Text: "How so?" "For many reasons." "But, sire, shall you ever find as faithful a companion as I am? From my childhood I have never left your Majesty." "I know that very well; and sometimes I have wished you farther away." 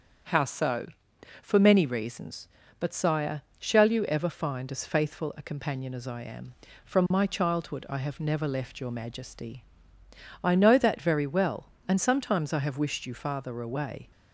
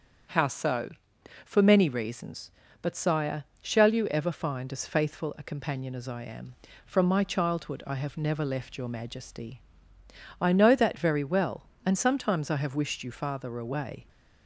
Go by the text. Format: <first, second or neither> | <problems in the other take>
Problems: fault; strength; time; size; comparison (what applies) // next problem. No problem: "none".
neither | starts louder than the rest; strong; the same in both